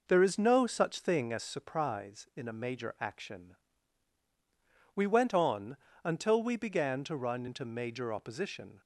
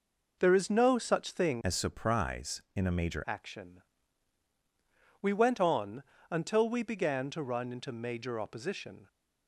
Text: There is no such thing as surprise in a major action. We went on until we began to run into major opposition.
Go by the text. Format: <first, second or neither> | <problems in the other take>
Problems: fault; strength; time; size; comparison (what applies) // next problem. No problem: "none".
first | changes voice from "as" to "major"; from 1.6 to 3.2 s; 1.6 s long // pauses between "on" and "until"; slight; at 6.0 s; 0.26 s long; slight in the first